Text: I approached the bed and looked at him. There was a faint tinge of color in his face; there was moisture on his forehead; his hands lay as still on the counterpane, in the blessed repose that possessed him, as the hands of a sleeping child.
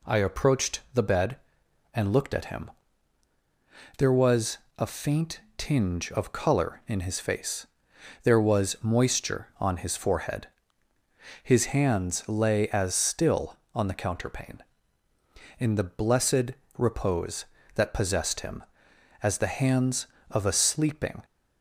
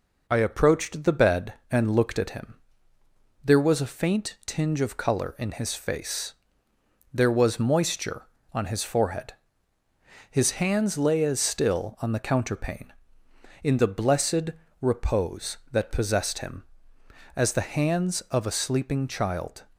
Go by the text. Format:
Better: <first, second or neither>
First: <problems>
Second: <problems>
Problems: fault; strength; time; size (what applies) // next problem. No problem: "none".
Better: second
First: pauses between "was" and "a"; slight; at 4.5 s; 0.20 s long // pauses between "faint" and "tinge"; slight; at 5.3 s; 0.18 s long // pauses between "blessed" and "repose"; slight; at 16.5 s; 0.24 s long // stops before "child"; at 21.2 s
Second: pauses between "blessed" and "repose"; slight; at 14.5 s; 0.30 s long